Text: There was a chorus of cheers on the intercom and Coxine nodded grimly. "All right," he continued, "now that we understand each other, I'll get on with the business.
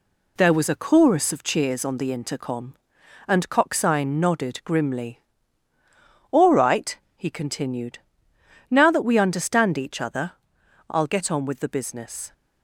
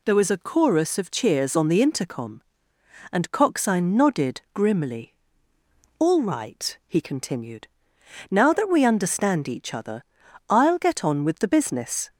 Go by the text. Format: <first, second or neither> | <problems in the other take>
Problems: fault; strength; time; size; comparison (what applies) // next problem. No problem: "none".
second | gets quieter; noticeable; throughout; 4.5 dB